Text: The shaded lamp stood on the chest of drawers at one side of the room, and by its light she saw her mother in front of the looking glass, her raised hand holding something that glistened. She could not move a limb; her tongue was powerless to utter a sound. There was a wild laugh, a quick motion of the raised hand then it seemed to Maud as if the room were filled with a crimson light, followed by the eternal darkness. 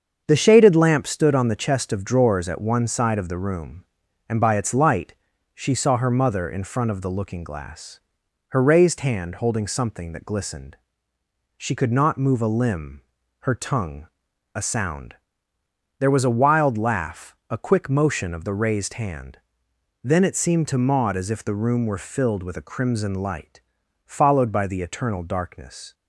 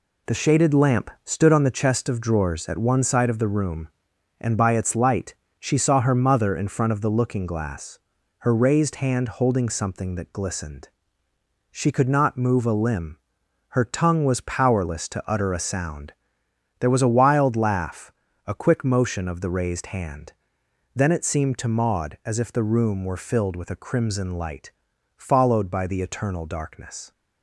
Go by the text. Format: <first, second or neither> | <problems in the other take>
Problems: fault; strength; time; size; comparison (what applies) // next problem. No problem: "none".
second | starts louder than the rest; strong; until 1.2 s; 7 dB // pauses between "light" and "she"; at 5.1 s; 0.38 s long; slight in the second // skips "was powerless to utter"; at 14.3 s // pauses between "hand" and "then"; noticeable; at 19.3 s; 0.66 s long; noticeable in the second